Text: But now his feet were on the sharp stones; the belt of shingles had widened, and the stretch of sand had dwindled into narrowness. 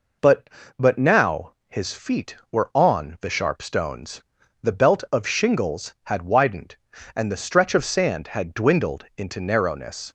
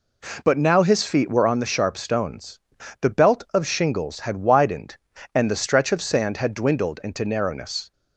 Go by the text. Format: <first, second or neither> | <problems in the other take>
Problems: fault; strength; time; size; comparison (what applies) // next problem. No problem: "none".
second | says "But" twice; at 0.7 s // pauses between "now" and "his"; slight; at 1.5 s; 0.16 s long